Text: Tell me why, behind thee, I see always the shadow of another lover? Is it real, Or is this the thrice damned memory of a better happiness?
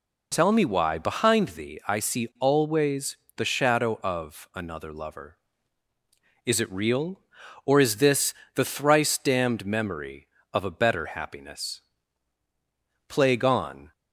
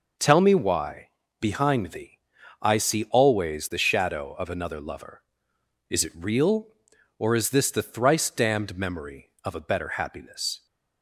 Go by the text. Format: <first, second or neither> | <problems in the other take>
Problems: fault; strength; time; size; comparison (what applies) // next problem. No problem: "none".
second | pauses between "always" and "the"; slight; at 3.1 s; 0.22 s long // pauses between "this" and "the"; slight; at 8.3 s; 0.20 s long // goes on to say "Plague on"; noticeable; from 13.0 s on; 0.84 s long